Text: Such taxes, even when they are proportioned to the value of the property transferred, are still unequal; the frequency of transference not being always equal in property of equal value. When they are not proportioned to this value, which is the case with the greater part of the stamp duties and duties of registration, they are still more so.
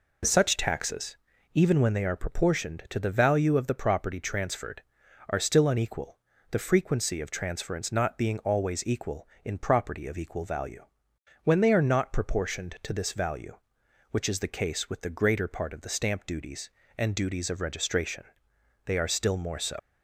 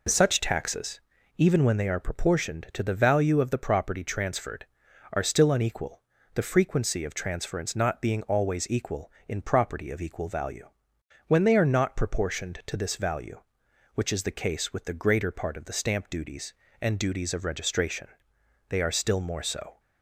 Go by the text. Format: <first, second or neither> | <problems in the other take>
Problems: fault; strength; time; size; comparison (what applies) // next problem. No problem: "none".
second | leaves "so" unfinished; at 19.7 s; 165 ms